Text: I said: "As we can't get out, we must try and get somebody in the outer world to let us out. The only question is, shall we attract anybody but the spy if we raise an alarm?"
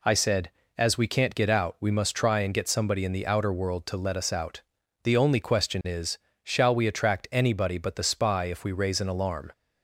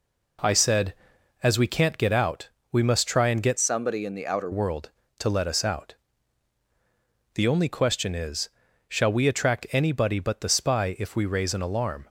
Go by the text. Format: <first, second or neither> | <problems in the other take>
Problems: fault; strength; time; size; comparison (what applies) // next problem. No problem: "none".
first | changes voice from "somebody" to "outer"; from 3.5 to 4.4 s; 0.9 s long